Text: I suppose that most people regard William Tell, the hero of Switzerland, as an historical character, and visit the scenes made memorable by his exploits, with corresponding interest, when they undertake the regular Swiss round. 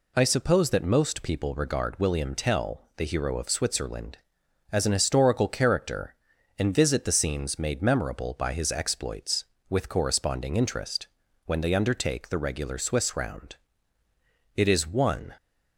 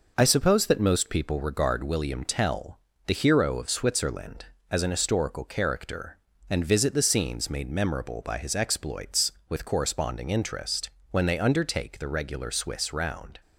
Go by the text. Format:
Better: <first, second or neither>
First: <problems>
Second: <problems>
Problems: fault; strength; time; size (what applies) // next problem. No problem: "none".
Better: second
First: goes on to say "It is one"; noticeable; from 14.5 s on; 0.78 s long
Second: none